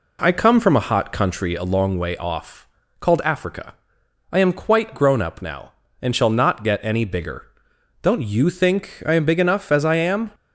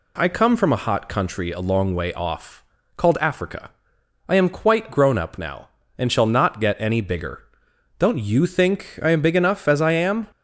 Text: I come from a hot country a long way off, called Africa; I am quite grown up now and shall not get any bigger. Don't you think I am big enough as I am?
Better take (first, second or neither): second